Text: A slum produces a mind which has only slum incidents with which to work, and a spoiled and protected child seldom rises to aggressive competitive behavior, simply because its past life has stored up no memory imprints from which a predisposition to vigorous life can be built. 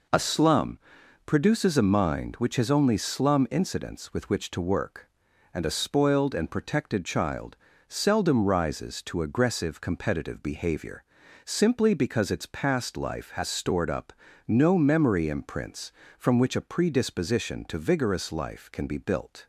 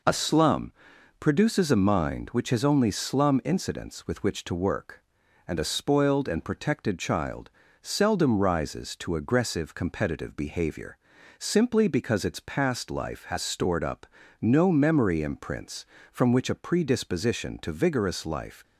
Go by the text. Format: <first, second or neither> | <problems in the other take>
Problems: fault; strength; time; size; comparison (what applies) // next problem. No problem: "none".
first | pauses between "slum" and "produces"; noticeable; at 0.7 s; 0.48 s long; noticeable in the first // pauses between "child" and "seldom"; slight; at 7.4 s; 0.32 s long; slight in the first // pauses between "up" and "no"; slight; at 14.0 s; 0.32 s long; slight in the first // stops before "can be built"; at 18.6 s